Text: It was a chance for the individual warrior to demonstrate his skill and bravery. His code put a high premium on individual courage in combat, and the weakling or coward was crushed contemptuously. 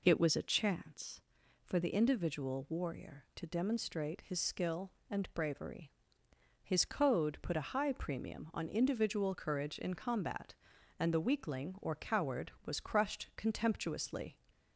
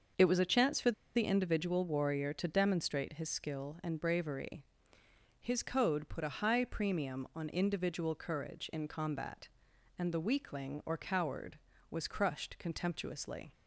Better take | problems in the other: first | starts louder than the rest; until 1.4 s; 6.5 dB // pauses between "for" and "the"; slight; at 0.9 s; 0.22 s long

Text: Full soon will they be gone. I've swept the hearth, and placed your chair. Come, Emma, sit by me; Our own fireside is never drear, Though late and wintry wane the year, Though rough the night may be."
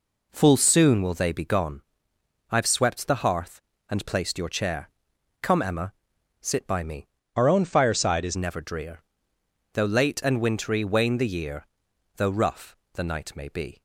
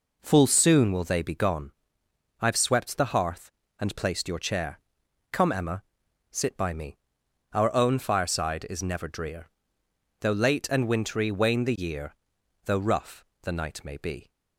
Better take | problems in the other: second | changes voice from "Our" to "is"; from 7.3 to 8.3 s; 1.0 s long // pauses between "rough" and "the"; slight; at 12.7 s; 0.16 s long; slight in the second

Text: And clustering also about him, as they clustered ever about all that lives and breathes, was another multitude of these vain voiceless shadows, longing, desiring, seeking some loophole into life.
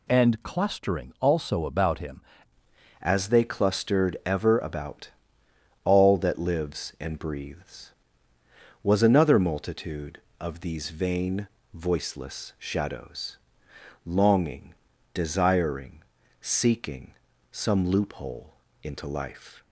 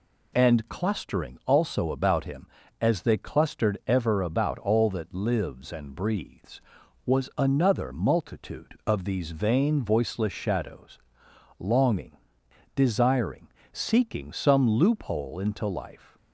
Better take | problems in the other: second | changes voice at "as"; from 3.0 s on; 16.6 s long // pauses between "about" and "all"; noticeable; at 5.1 s; 0.74 s long // pauses between "vain" and "voiceless"; slight; at 11.4 s; 0.26 s long // pauses between "seeking" and "some"; at 17.1 s; 0.38 s long // pauses between "loophole" and "into"; slight; at 18.5 s; 0.28 s long

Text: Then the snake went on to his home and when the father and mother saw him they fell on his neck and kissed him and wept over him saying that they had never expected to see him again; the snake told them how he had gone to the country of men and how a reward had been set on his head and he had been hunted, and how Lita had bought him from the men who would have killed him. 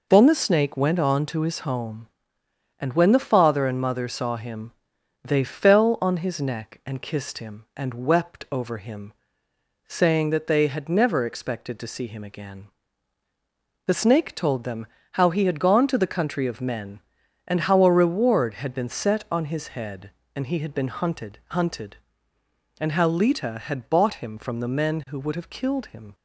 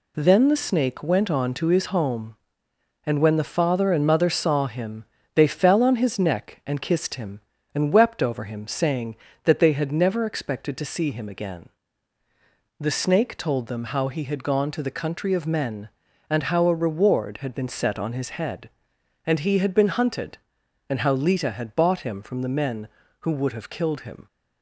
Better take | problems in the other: second | pauses between "him" and "they"; noticeable; at 4.7 s; 0.52 s long; slight in the second // pauses between "him" and "saying"; noticeable; at 9.1 s; 0.74 s long // pauses between "them" and "how"; slight; at 14.8 s; 0.26 s long // says "hunted" twice; at 21.4 s

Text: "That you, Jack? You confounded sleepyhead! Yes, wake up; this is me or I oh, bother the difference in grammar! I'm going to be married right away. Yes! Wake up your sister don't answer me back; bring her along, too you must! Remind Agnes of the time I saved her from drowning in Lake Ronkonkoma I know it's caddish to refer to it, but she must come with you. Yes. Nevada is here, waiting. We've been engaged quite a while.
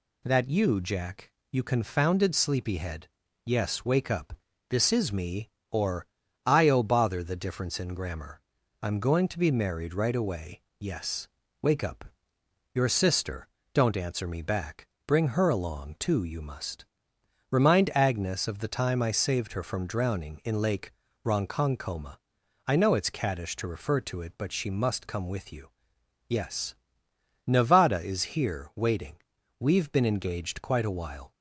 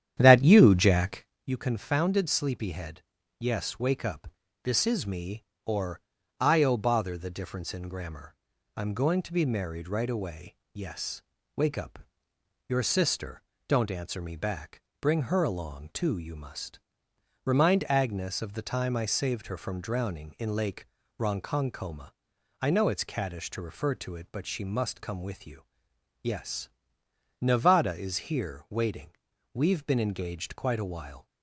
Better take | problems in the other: first | starts louder than the rest; strong; until 1.3 s; 10 dB // pauses between "or" and "I"; at 6.0 s; 0.40 s long; also in the first // pauses between "up" and "your"; noticeable; at 12.0 s; 0.68 s long; noticeable in the first // pauses between "sister" and "don't"; slight; at 13.4 s; 0.26 s long; slight in the first // pauses between "Lake" and "Ronkonkoma"; slight; at 20.8 s; 0.34 s long; slight in the first // pauses between "Ronkonkoma" and "I"; noticeable; at 22.1 s; 0.50 s long; noticeable in the first

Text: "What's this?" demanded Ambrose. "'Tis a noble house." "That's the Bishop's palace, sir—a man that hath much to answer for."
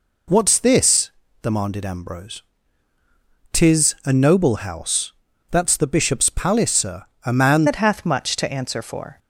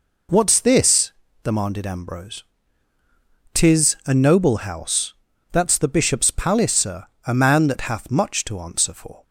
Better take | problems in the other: second | changes voice at "that"; from 7.6 s on; 1.5 s long

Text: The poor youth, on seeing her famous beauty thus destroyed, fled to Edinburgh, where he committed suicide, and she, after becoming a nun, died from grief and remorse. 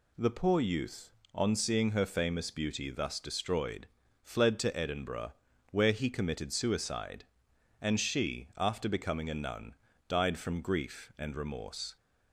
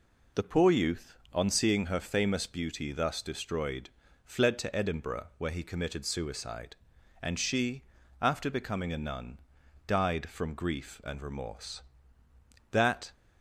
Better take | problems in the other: first | goes on to say "That"; slight; from 12.7 s on; 0.40 s long

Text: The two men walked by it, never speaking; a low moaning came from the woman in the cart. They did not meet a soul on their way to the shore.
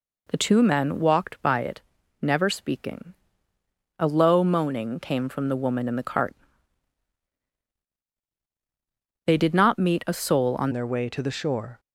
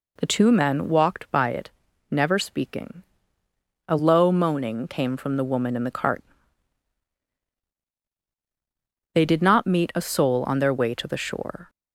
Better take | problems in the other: second | changes voice at "their"; from 10.7 s on; 1.0 s long

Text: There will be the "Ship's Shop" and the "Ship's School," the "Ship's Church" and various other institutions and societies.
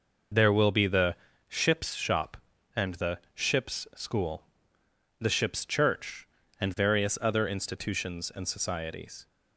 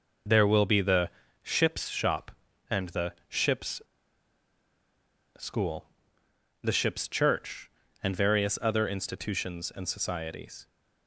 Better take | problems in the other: first | pauses between "the" and "Ship's"; slight; at 1.0 s; 0.32 s long; slight in the first // pauses between "the" and "Ship's"; slight; at 3.1 s; 0.16 s long; slight in the first // pauses between "Ship's" and "School"; strong; at 3.8 s; 1.5 s long

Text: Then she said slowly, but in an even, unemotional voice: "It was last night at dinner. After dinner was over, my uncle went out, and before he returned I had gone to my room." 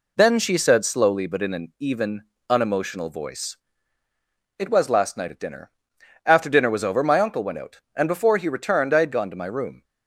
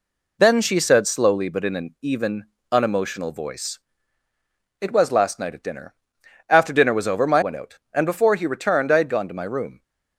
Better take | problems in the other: first | skips "uncle"; at 7.4 s

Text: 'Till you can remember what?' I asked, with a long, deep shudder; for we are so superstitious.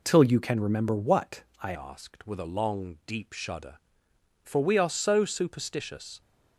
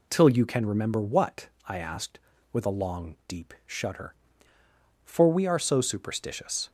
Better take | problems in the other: second | changes voice at "asked"; from 1.7 s on; 4.5 s long

